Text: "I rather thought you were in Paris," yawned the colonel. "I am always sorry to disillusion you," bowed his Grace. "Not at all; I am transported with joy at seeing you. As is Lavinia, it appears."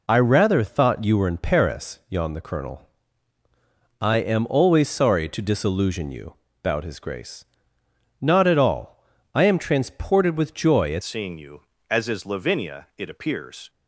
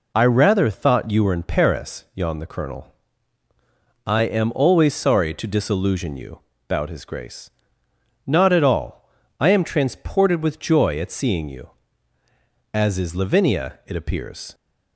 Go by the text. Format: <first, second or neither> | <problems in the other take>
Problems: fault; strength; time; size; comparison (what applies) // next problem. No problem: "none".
second | changes voice at "seeing"; from 11.0 s on; 2.6 s long